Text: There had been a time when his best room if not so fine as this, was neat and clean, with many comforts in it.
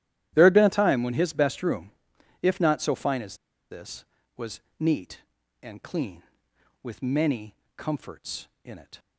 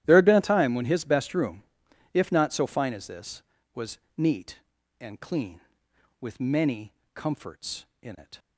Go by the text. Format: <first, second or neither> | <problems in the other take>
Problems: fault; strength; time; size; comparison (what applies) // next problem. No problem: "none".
second | starts louder than the rest; strong; until 1.3 s; 12.5 dB; strong in the second // pauses between "room" and "if"; noticeable; at 1.9 s; 0.50 s long; noticeable in the second // pauses between "as" and "this"; slight; at 3.3 s; 0.33 s long // pauses between "was" and "neat"; slight; at 4.6 s; 0.18 s long; slight in the second // pauses between "many" and "comforts"; slight; at 7.5 s; 0.20 s long; slight in the second